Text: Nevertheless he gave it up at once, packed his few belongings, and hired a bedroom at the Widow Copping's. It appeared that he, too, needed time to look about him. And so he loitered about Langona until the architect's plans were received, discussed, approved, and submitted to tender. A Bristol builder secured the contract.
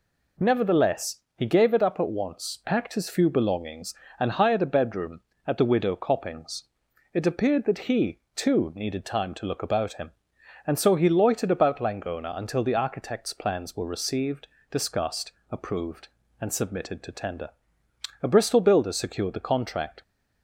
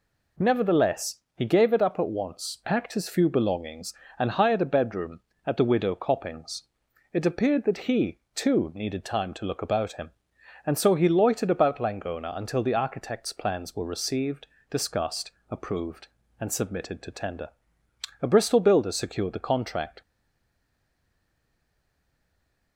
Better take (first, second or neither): first